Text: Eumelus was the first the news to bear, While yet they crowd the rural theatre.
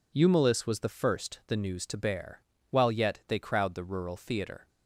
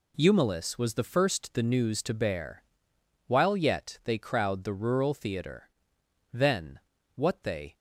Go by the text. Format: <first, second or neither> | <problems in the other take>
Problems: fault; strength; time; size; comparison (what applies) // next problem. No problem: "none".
first | goes on to say "Then what they"; from 6.3 s on; 1.4 s long